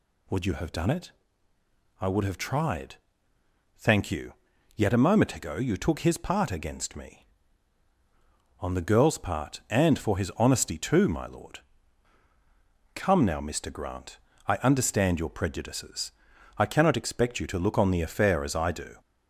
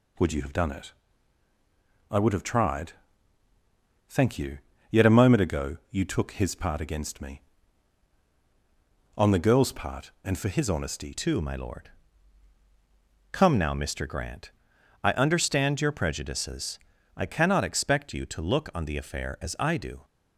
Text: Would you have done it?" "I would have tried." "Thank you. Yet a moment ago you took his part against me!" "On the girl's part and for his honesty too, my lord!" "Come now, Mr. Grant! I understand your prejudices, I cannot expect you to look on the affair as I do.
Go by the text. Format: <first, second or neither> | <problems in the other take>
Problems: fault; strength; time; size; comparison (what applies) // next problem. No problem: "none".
first | changes voice at "too"; from 11.1 s on; 8.9 s long